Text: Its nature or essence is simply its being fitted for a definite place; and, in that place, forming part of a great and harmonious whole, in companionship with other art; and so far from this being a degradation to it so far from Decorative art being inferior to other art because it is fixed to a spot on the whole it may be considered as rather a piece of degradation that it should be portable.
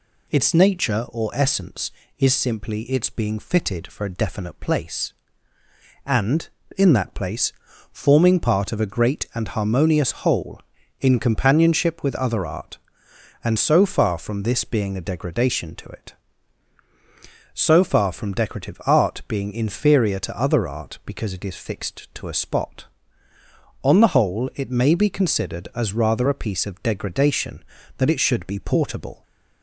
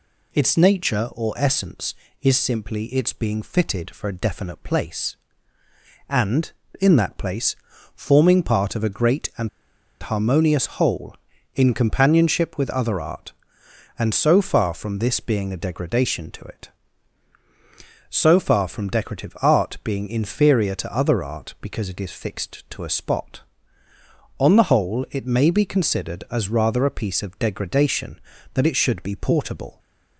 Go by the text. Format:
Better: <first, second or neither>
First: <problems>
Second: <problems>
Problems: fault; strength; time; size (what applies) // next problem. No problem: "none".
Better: first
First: none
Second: pauses between "and" and "harmonious"; noticeable; at 9.4 s; 0.53 s long